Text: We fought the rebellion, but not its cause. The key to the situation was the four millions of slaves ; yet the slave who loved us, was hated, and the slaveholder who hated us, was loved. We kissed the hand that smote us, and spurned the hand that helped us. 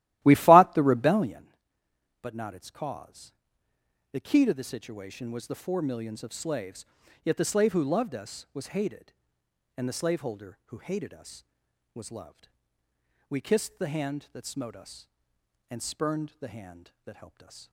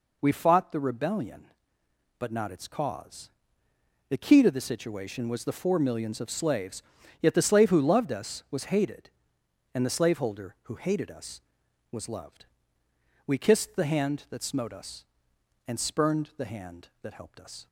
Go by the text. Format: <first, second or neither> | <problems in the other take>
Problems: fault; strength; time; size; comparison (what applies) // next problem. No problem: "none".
second | starts louder than the rest; strong; until 1.5 s; 15 dB